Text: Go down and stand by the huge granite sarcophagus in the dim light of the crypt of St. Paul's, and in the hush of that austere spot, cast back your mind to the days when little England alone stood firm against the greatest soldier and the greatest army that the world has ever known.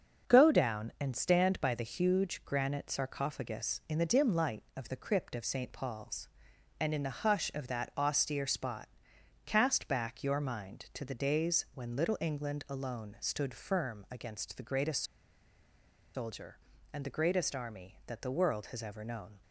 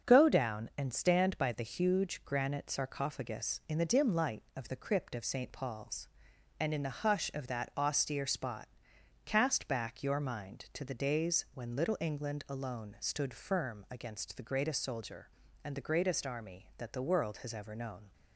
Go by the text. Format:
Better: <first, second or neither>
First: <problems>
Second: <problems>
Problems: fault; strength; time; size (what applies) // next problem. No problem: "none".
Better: second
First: starts louder than the rest; until 1.3 s; 6.5 dB // pauses between "greatest" and "soldier"; at 15.0 s; 1.1 s long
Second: starts louder than the rest; until 1.1 s; 6.5 dB